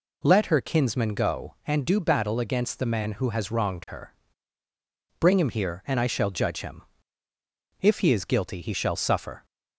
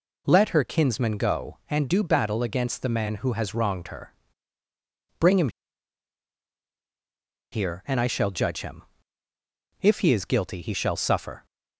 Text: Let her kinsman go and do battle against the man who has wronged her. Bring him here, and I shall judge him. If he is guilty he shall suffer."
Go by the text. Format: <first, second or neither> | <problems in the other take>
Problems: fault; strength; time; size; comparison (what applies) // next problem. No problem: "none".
first | pauses between "him" and "here"; strong; at 5.4 s; 2.0 s long